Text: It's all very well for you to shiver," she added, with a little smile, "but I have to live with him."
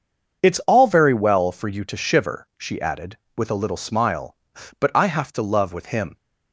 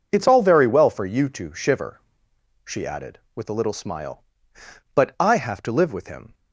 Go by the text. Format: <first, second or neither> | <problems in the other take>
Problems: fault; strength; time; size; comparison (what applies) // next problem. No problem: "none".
second | starts louder than the rest; until 1.4 s; 6.5 dB // says "love" for "live"; at 5.4 s